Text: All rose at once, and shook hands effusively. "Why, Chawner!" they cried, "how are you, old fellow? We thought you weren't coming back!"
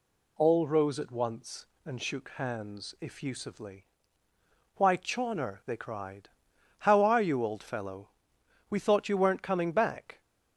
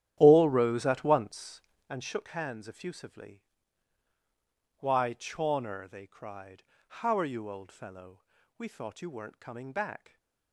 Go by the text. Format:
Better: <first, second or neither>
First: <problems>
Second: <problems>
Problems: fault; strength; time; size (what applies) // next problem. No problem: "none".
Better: first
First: none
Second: starts louder than the rest; strong; until 2.0 s; 11 dB